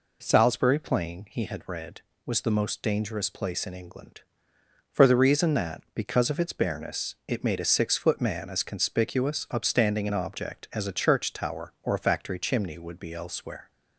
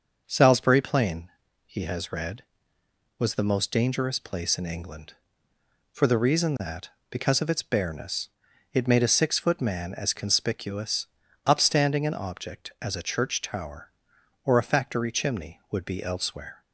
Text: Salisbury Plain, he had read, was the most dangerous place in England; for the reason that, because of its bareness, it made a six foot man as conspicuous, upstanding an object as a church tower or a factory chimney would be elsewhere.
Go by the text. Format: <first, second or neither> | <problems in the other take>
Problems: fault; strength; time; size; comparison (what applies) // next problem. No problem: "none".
first | starts louder than the rest; until 1.2 s; 6 dB // says "has" for "had"; at 1.8 s